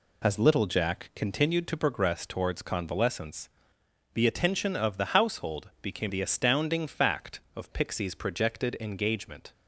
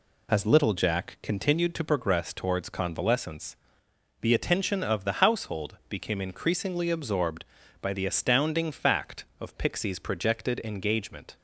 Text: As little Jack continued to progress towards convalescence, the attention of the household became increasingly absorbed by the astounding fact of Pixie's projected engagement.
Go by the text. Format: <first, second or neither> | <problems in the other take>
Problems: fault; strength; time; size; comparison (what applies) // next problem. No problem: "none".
second | skips "increasingly absorbed by"; at 6.0 s